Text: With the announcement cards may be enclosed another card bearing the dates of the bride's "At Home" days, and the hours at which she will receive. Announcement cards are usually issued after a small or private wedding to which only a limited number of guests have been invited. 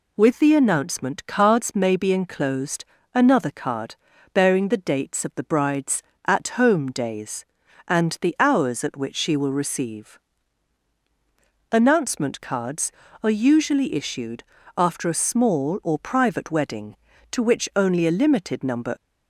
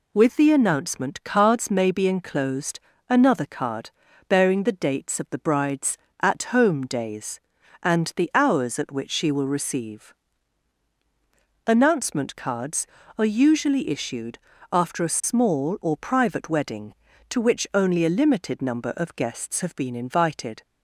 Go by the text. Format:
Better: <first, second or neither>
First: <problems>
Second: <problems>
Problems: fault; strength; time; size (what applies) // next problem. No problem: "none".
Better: second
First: pauses between "enclosed" and "another"; slight; at 2.8 s; 0.28 s long // pauses between "card" and "bearing"; at 3.9 s; 0.38 s long // pauses between "issued" and "after"; slight; at 14.4 s; 0.34 s long // stops before "of guests have been invited"; at 18.9 s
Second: pauses between "enclosed" and "another"; slight; at 2.8 s; 0.28 s long // pauses between "card" and "bearing"; at 3.9 s; 0.38 s long // pauses between "issued" and "after"; slight; at 14.3 s; 0.34 s long